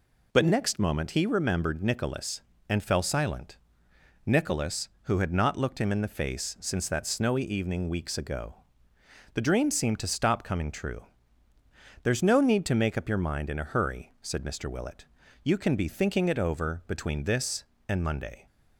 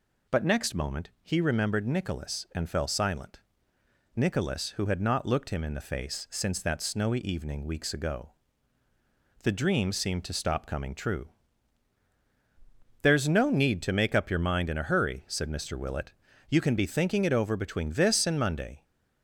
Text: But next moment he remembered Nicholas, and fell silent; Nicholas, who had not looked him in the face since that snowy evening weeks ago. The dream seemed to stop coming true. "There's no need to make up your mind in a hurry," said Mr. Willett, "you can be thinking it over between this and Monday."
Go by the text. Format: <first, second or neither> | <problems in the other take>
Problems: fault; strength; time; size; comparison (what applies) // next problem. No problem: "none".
neither | none